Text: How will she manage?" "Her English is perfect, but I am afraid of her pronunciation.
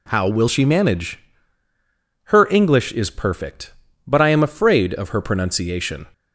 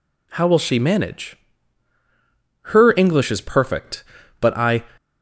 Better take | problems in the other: first | stops before "am afraid of her pronunciation"; at 4.9 s

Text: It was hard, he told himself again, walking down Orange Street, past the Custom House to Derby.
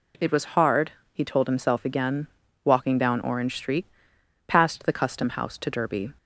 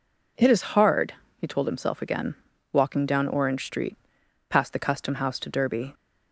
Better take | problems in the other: first | says "is" for "was"; at 0.4 s

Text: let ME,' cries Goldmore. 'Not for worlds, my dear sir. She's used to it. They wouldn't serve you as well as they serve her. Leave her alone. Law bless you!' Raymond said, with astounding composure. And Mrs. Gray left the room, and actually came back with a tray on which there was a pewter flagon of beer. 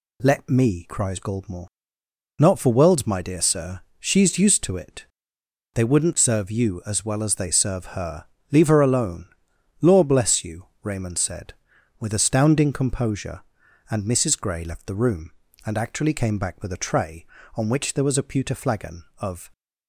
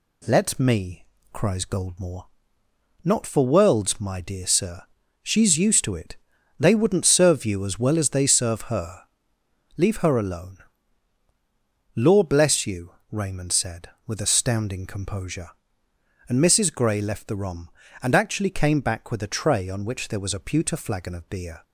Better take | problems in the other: second | stops before "beer"; at 19.5 s

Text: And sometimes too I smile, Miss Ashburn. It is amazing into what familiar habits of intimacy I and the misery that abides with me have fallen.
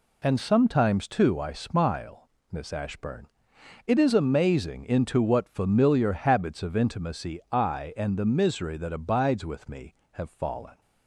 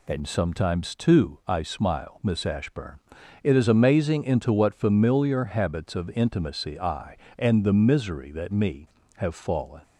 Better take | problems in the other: first | skips "abides with"; at 8.4 s

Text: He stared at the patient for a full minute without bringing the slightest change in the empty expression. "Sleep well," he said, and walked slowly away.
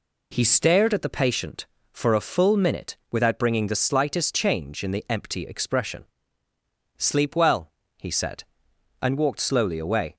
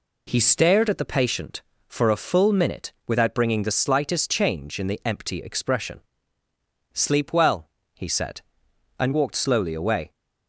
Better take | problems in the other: neither | none

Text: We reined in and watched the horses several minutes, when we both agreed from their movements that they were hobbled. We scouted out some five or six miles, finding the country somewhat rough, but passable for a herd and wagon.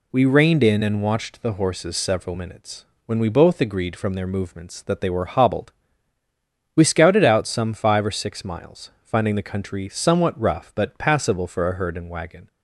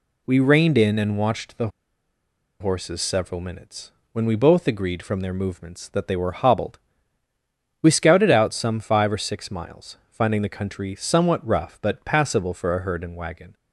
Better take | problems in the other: first | pauses between "the" and "horses"; noticeable; at 1.6 s; 0.91 s long

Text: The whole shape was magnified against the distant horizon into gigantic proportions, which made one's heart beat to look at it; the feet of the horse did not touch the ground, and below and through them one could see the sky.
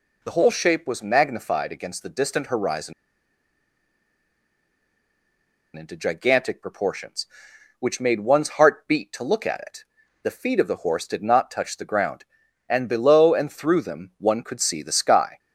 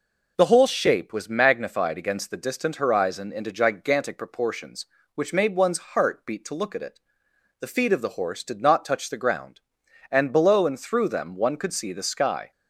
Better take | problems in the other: second | pauses between "horizon" and "into"; strong; at 2.9 s; 2.8 s long

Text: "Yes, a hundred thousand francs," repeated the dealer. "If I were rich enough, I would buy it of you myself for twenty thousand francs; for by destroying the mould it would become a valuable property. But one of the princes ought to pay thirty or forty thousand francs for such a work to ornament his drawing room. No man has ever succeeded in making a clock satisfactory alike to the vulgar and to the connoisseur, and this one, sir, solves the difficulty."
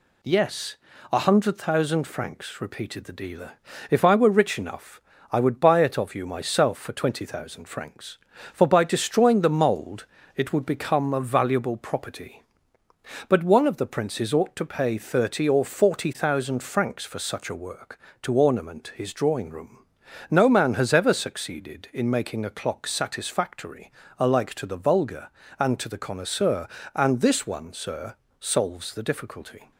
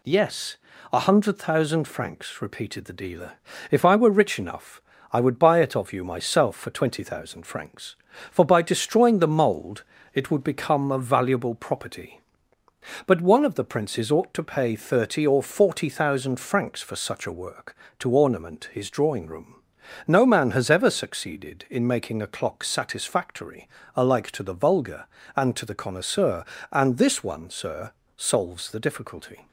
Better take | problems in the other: neither | pauses between "mould" and "it"; slight; the same in both // pauses between "satisfactory" and "alike"; slight; the same in both

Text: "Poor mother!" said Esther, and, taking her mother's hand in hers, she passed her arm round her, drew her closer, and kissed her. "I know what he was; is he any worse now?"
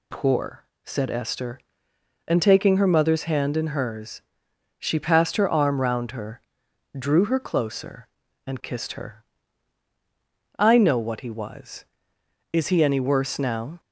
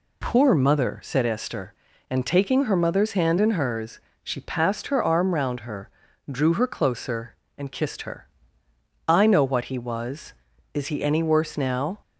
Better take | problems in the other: second | skips "mother"; at 0.7 s

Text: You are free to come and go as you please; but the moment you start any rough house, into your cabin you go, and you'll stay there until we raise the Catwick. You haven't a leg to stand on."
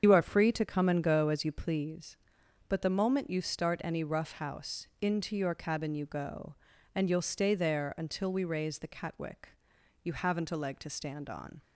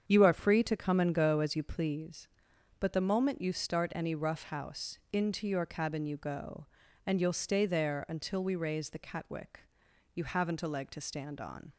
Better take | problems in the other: second | loses the start of "You"; at 0.0 s; 70 ms // starts louder than the rest; strong; until 1.0 s; 7.5 dB; strong in the second

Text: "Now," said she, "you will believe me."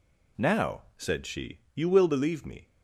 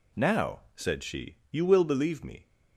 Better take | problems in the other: neither | none

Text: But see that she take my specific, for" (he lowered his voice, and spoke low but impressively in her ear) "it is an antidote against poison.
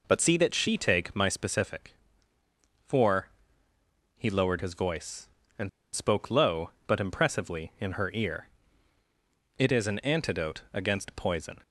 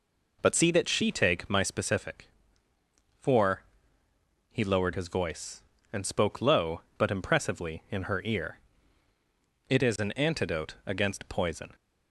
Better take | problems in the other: second | pauses between "and" and "spoke"; slight; at 5.6 s; 0.24 s long

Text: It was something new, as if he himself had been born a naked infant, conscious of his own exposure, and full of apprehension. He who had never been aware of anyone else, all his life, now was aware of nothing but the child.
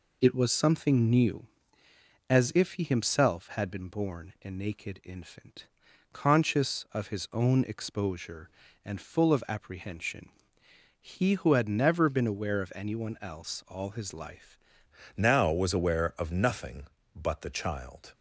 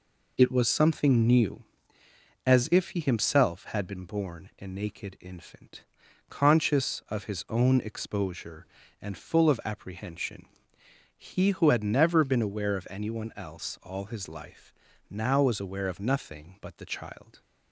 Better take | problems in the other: second | changes voice at "now"; from 15.1 s on; 3.0 s long

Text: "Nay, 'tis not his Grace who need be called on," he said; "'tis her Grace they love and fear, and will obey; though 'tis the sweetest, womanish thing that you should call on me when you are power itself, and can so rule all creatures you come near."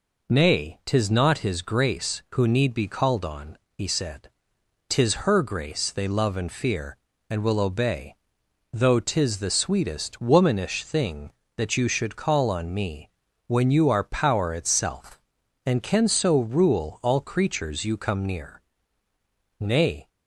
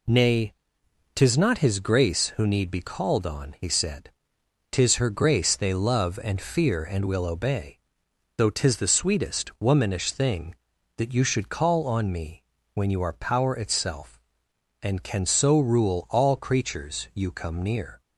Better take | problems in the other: second | pauses between "me" and "when"; at 13.0 s; 0.38 s long; slight in the second // goes on to say "Nay"; slight; from 19.6 s on; 0.48 s long

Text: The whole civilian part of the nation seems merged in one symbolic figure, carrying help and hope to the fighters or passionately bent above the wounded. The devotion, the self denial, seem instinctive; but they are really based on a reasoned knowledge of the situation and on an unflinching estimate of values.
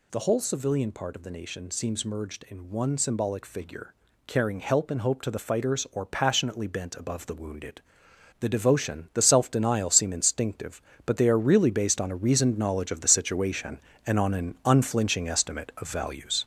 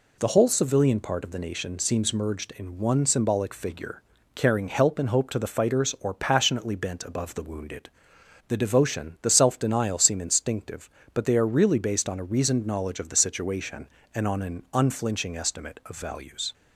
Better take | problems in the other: second | gets louder; noticeable; throughout; 6 dB

